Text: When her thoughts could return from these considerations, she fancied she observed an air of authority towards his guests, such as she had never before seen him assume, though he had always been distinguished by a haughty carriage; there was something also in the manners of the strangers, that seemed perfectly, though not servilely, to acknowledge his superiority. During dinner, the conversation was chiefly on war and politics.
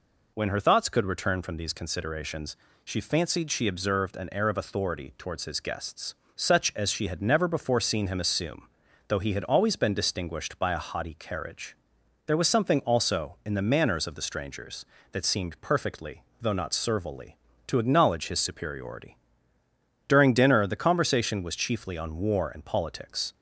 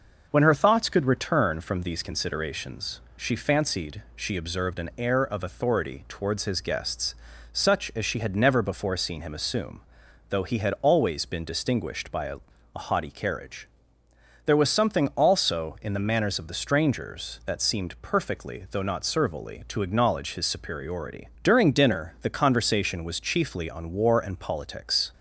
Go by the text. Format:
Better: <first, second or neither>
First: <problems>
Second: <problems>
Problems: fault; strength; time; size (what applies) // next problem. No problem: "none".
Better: first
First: none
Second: says "a" twice; at 12.7 s